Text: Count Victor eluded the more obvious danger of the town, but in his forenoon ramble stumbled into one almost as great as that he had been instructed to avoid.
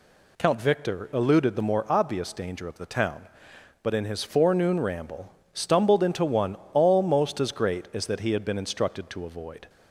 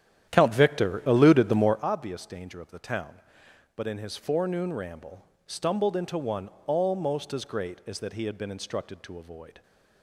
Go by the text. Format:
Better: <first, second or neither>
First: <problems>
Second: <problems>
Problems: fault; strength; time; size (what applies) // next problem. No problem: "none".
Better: first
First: pauses between "ramble" and "stumbled"; slight; at 5.3 s; 0.22 s long // pauses between "one" and "almost"; slight; at 6.5 s; 0.18 s long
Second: starts louder than the rest; strong; until 1.9 s; 10.5 dB // pauses between "ramble" and "stumbled"; slight; at 5.2 s; 0.22 s long // pauses between "one" and "almost"; slight; at 6.4 s; 0.18 s long